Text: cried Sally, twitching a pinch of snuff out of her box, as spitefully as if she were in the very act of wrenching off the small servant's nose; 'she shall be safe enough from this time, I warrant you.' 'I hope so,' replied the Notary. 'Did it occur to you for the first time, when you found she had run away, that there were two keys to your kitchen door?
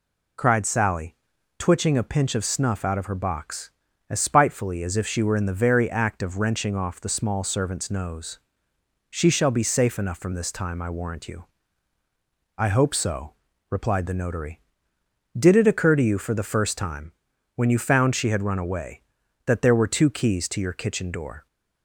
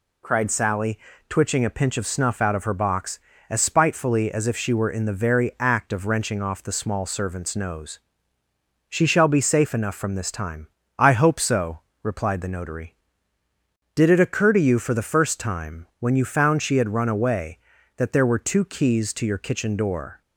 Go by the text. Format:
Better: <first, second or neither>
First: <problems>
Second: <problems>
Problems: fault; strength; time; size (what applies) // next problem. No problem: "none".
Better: first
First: none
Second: skips "I warrant you"; at 10.8 s